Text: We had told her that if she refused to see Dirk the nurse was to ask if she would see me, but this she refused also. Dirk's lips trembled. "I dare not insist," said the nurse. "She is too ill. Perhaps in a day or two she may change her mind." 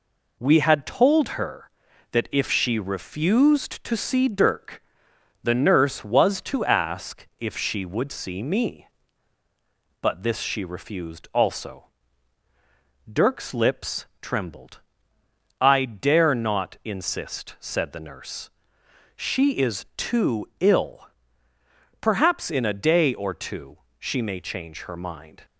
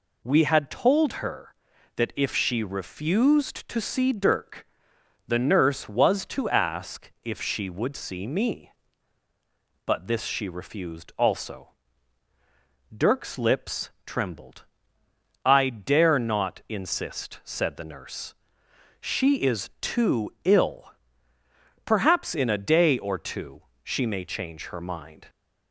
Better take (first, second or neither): second